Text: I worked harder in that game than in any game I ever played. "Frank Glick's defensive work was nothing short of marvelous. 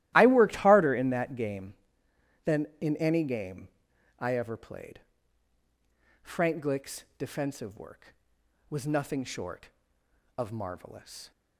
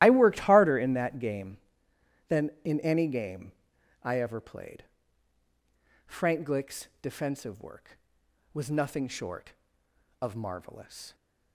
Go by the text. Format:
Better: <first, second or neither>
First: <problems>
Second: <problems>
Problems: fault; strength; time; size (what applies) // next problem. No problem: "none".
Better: first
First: starts louder than the rest; strong; until 1.1 s; 15 dB // pauses between "game" and "I"; noticeable; at 3.6 s; 0.50 s long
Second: loses the start of "I"; at 0.0 s; 30 ms // starts louder than the rest; strong; until 1.0 s; 14.5 dB // pauses between "game" and "I"; noticeable; at 3.5 s; 0.50 s long